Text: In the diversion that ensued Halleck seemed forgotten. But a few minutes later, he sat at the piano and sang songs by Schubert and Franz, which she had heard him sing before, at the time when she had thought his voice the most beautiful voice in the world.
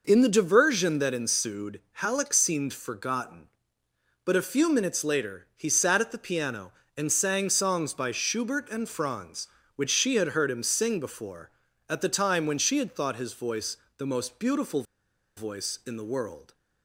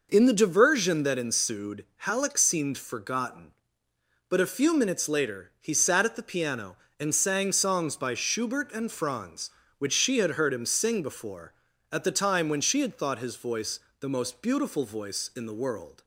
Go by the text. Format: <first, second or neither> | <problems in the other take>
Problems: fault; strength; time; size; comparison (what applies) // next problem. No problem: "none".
second | pauses between "voice" and "the"; slight; at 13.7 s; 0.20 s long; slight in the second // pauses between "beautiful" and "voice"; noticeable; at 14.8 s; 0.53 s long